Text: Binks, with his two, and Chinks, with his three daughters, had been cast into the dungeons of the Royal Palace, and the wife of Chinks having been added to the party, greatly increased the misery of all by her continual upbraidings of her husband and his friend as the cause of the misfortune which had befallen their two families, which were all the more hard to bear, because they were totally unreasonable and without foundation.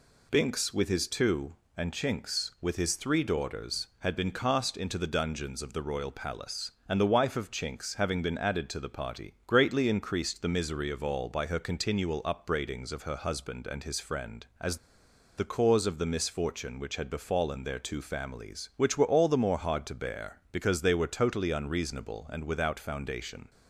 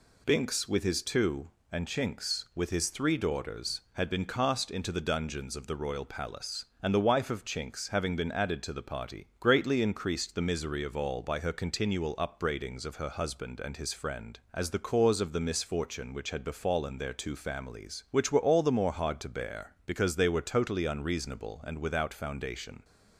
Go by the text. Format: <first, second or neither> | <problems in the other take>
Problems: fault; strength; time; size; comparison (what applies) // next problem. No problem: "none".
second | pauses between "as" and "the"; noticeable; at 14.7 s; 0.60 s long